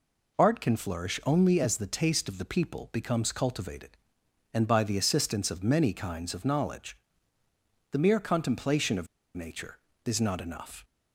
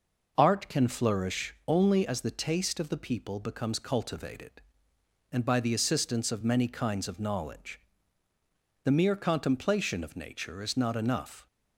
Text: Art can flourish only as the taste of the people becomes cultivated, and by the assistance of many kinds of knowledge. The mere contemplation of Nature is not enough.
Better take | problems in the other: second | pauses between "of" and "Nature"; slight; at 9.0 s; 0.28 s long

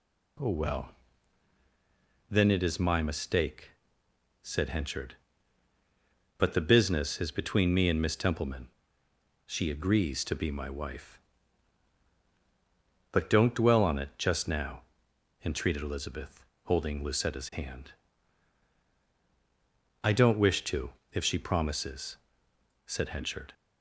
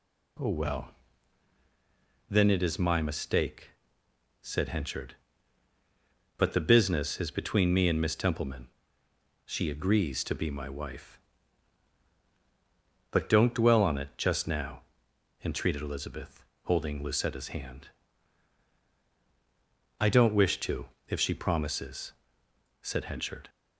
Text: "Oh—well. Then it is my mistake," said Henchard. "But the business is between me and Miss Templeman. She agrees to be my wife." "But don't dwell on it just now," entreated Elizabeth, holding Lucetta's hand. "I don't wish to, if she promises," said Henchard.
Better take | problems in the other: neither | none

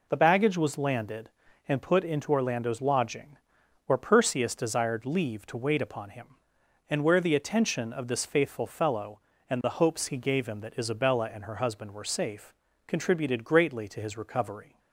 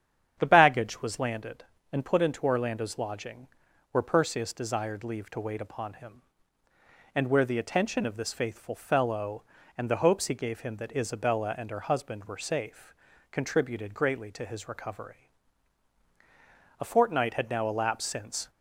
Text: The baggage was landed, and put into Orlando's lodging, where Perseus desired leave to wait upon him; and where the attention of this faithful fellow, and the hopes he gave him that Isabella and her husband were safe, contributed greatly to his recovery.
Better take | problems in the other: first | starts louder than the rest; strong; until 1.4 s; 8.5 dB // goes on to say "A fortnight had now elapsed since"; strong; from 16.8 s on; 1.6 s long

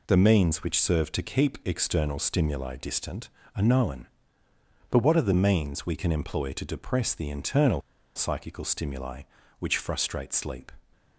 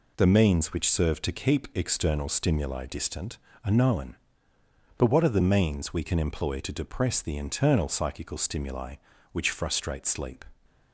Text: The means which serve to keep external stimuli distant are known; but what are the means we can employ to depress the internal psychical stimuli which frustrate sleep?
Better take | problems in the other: second | pauses between "internal" and "psychical"; slight; at 7.8 s; 0.34 s long

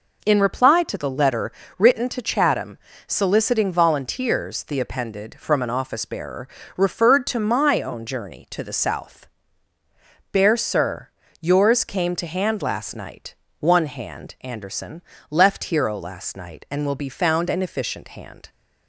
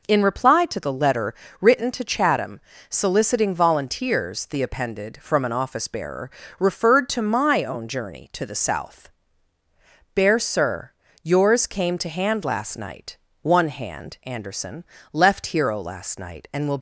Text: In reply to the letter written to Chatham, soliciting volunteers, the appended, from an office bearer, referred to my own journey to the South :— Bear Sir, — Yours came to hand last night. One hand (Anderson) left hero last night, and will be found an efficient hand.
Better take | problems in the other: first | pauses between "letter" and "written"; slight; at 1.3 s; 0.26 s long; slight in the first // stops before "be found an efficient hand"; at 16.7 s

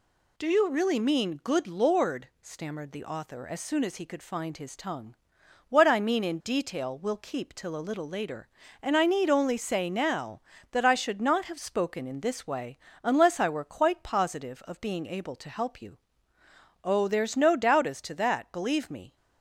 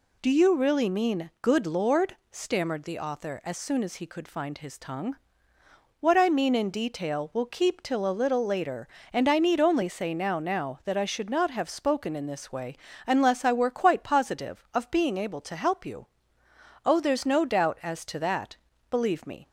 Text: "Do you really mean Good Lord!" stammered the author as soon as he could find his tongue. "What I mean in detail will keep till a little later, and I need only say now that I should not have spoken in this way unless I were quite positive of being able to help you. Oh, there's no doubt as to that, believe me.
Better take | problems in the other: first | says "now" twice; at 10.3 s // pauses between "way" and "unless"; slight; at 12.7 s; 0.29 s long; slight in the first

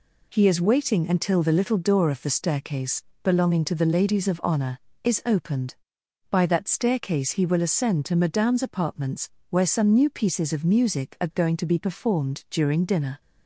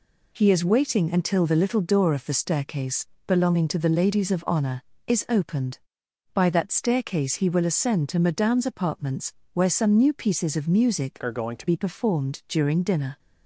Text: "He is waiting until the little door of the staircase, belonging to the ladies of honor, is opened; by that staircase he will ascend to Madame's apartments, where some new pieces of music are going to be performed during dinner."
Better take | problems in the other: first | changes voice from "are" to "to"; from 11.2 to 11.6 s; 0.4 s long

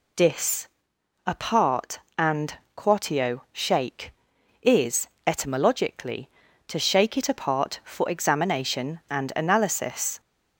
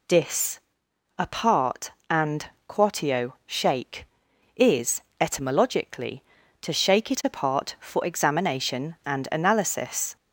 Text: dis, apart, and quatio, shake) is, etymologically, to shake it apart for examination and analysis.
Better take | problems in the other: neither | pauses between "and" and "quatio"; slight; the same in both

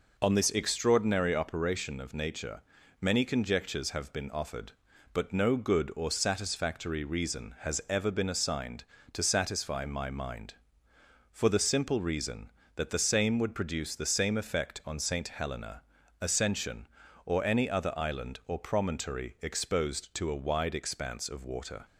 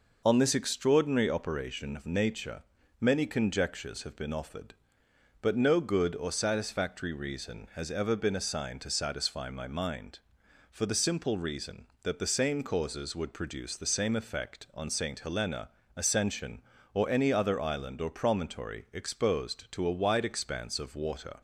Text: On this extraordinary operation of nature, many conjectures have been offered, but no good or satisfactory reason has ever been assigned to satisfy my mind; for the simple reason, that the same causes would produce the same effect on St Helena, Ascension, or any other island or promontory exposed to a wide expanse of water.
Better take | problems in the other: second | skips "causes"; at 13.3 s

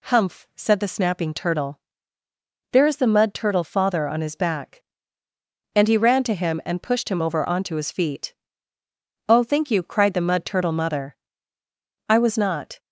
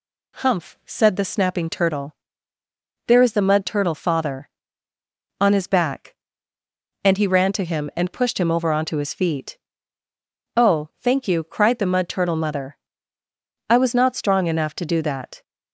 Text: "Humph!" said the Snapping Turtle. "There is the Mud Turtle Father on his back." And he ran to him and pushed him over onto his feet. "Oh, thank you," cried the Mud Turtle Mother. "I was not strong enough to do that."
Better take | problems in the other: second | stops before "strong enough to do that"; at 12.7 s

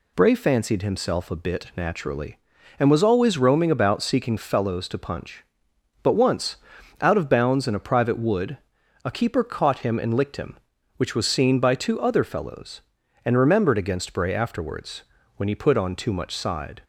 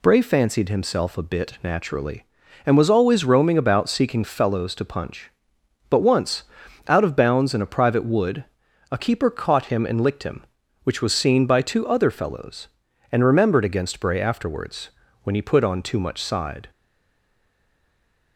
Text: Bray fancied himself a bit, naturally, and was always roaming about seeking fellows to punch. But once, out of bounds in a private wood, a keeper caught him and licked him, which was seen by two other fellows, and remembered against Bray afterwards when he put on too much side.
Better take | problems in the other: first | pauses between "afterwards" and "when"; slight; at 14.8 s; 0.36 s long; slight in the first // stays silent after the last word; noticeable; from 16.7 s on; 1.6 s long

